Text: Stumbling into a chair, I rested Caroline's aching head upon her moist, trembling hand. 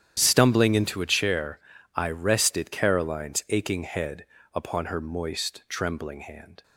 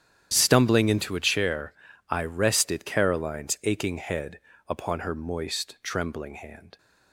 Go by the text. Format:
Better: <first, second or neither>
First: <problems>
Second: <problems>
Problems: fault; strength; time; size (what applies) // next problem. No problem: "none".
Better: neither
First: starts louder than the rest; strong; until 1.1 s; 10 dB // pauses between "head" and "upon"; slight; at 4.2 s; 0.26 s long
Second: starts louder than the rest; strong; until 1.3 s; 10 dB // pauses between "head" and "upon"; slight; at 4.4 s; 0.26 s long